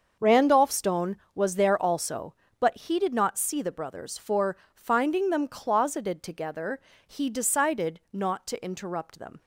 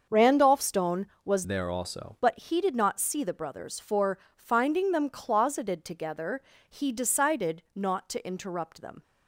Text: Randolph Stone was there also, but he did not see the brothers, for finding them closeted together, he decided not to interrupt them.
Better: first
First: starts louder than the rest; until 1.4 s; 6.5 dB // pauses between "for" and "finding"; slight; at 4.5 s; 0.16 s long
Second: starts louder than the rest; until 1.3 s; 6.5 dB // changes voice from "there" to "also"; from 1.4 to 2.1 s; 0.7 s long // pauses between "for" and "finding"; slight; at 4.1 s; 0.16 s long

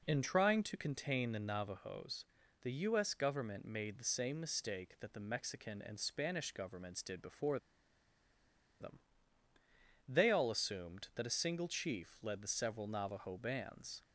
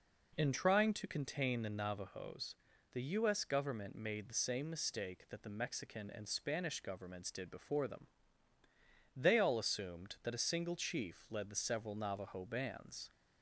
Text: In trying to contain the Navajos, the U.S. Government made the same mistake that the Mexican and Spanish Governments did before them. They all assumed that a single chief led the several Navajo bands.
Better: second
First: pauses between "before" and "them"; at 7.5 s; 1.2 s long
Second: none

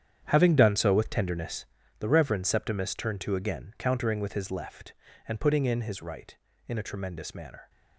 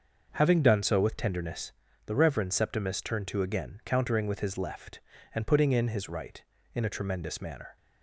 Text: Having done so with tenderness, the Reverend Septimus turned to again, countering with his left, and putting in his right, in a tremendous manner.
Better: second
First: gets quieter; strong; throughout; 12.5 dB // starts louder than the rest; strong; until 1.2 s; 9 dB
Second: starts louder than the rest; until 1.3 s; 6.5 dB

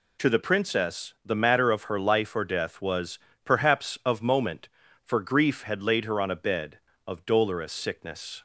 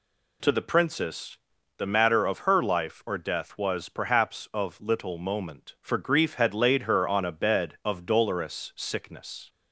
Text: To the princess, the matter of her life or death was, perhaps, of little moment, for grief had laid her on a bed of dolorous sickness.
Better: second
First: skips "little"; at 4.2 s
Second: none

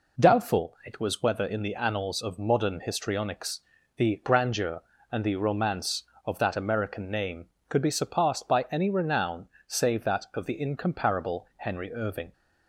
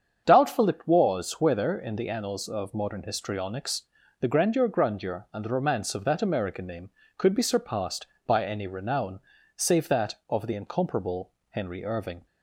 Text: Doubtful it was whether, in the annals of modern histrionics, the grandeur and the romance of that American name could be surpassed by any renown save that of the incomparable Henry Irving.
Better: first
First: pauses between "renown" and "save"; slight; at 9.4 s; 0.18 s long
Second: starts louder than the rest; strong; until 1.2 s; 7.5 dB // says "grandeur" twice; at 4.6 s // pauses between "renown" and "save"; slight; at 9.2 s; 0.36 s long // pauses between "incomparable" and "Henry"; slight; at 11.3 s; 0.20 s long

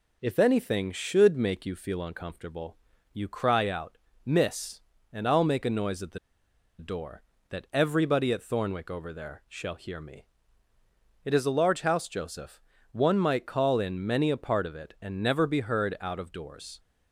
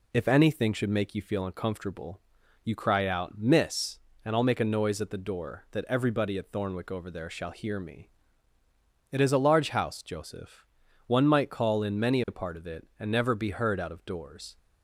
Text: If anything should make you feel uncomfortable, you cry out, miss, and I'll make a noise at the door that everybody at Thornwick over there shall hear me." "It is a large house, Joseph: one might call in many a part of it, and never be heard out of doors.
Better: second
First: pauses between "the" and "door"; noticeable; at 6.1 s; 0.60 s long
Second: none

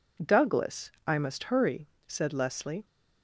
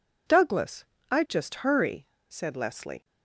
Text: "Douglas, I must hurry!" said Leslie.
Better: first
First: none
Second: says "just" for "must"; at 1.2 s

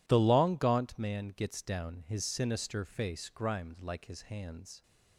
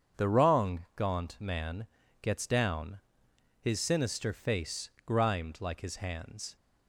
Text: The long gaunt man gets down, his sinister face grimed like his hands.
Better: first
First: none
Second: starts louder than the rest; strong; until 1.2 s; 7 dB // says "wrong" for "long"; at 0.2 s // pauses between "man" and "gets"; slight; at 1.8 s; 0.34 s long // pauses between "face" and "grimed"; slight; at 4.8 s; 0.16 s long

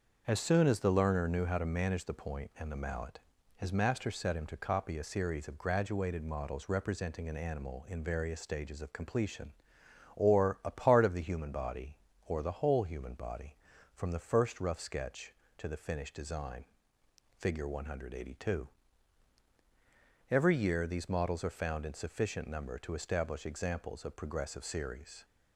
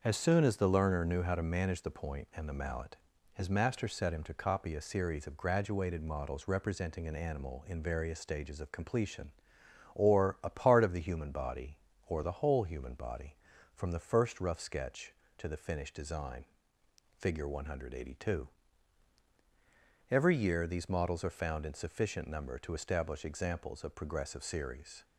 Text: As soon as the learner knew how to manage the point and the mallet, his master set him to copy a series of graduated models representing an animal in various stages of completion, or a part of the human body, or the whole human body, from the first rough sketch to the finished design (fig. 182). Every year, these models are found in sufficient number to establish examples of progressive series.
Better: neither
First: starts louder than the rest; until 1.2 s; 6.5 dB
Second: starts louder than the rest; until 1.0 s; 6.5 dB

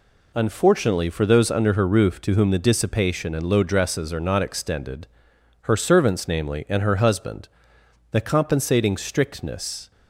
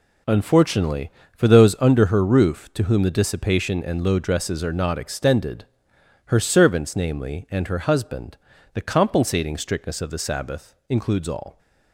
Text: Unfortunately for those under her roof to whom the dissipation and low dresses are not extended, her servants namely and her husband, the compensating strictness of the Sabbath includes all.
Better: second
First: stops before "of the Sabbath includes all"; at 9.9 s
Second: none

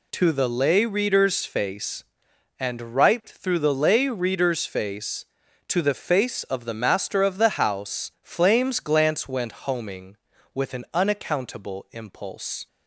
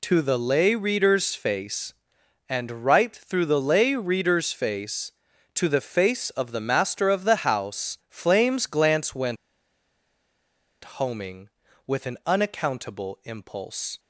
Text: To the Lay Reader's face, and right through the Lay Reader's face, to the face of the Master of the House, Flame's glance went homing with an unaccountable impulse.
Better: first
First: none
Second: pauses between "went" and "homing"; strong; at 9.3 s; 1.4 s long

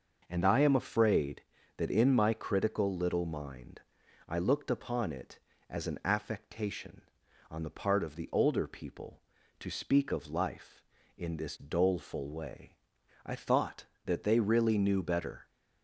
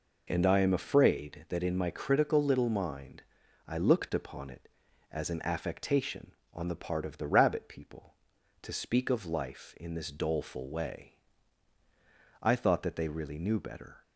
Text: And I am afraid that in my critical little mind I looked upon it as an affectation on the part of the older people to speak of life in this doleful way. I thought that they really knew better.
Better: first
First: pauses between "mind" and "I"; noticeable; at 3.8 s; 0.46 s long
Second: pauses between "mind" and "I"; at 3.2 s; 0.44 s long // says "rabbit" for "older"; at 7.2 s

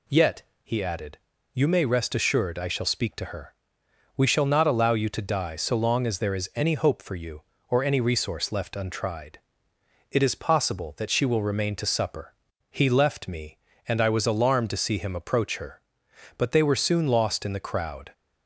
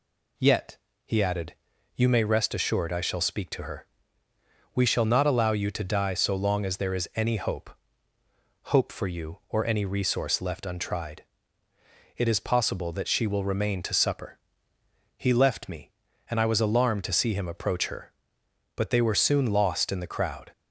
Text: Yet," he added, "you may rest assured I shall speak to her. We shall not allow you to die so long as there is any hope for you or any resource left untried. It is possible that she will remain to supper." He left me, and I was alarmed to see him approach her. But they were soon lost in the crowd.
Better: first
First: none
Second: says "hope" twice; at 8.6 s

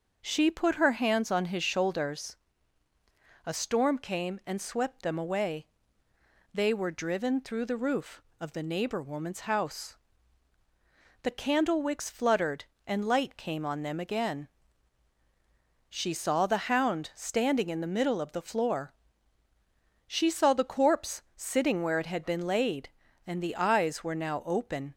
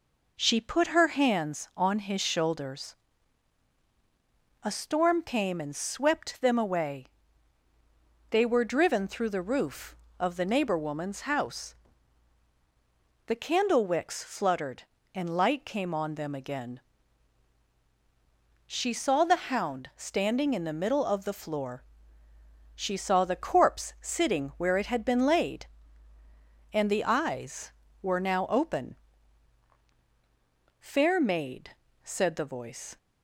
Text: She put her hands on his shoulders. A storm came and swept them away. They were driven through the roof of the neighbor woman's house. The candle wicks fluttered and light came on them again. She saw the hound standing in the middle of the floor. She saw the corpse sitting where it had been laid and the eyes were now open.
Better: first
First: none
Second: goes on to say "Fair Maid said the voice"; strong; from 30.7 s on; 2.1 s long

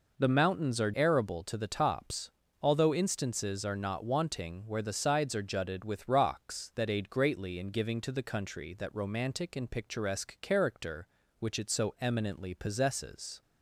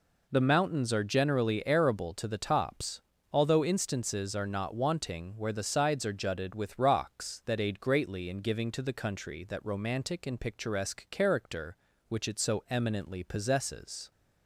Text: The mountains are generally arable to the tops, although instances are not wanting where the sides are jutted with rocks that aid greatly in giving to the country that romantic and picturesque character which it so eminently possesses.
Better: second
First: skips "generally"; at 0.9 s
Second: none

